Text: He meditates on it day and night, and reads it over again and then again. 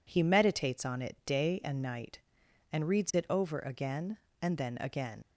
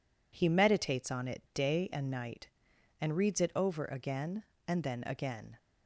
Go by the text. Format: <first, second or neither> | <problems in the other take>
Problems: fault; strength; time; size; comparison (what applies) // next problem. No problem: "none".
second | leaves "again" unfinished; at 5.2 s; 95 ms